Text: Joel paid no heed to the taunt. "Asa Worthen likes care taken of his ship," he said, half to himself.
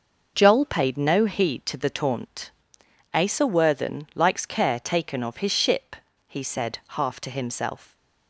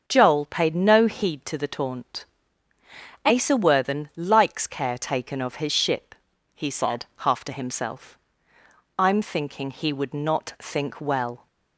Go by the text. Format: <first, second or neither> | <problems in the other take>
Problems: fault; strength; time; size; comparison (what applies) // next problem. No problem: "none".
first | starts louder than the rest; until 1.0 s; 6.5 dB // goes on to say "I'm thinking he would not think well"; strong; from 8.9 s on; 2.4 s long